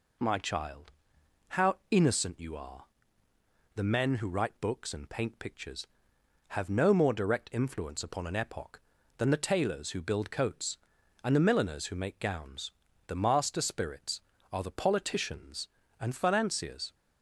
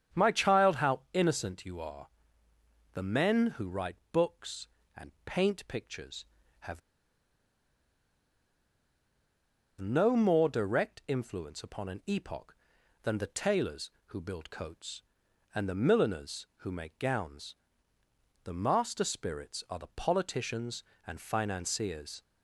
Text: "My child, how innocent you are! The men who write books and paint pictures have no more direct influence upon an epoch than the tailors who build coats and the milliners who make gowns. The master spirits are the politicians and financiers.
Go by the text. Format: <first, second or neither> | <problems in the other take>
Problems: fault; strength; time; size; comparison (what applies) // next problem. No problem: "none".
first | starts louder than the rest; strong; until 1.2 s; 8 dB // pauses between "write" and "books"; slight; at 3.9 s; 0.16 s long // pauses between "have" and "no"; strong; at 6.8 s; 3.0 s long